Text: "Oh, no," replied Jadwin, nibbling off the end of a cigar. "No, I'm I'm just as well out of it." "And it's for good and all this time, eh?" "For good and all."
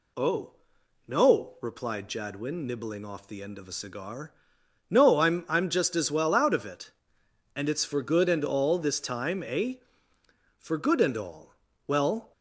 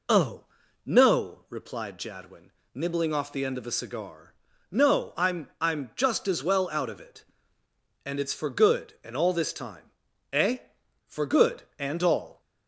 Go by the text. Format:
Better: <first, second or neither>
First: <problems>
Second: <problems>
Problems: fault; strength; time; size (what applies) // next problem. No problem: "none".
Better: second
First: goes on to say "Well"; slight; from 11.8 s on; 0.44 s long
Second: none